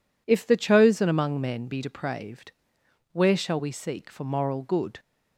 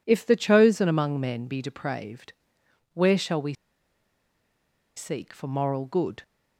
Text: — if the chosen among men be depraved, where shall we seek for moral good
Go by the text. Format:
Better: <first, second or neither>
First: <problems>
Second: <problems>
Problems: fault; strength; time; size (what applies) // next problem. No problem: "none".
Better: first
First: none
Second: pauses between "we" and "seek"; strong; at 3.5 s; 1.4 s long